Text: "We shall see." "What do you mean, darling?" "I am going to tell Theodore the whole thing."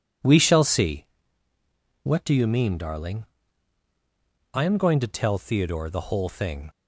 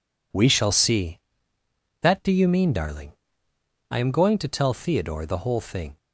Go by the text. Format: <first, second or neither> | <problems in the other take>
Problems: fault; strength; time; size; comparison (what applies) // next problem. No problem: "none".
first | says "That" for "What"; at 2.0 s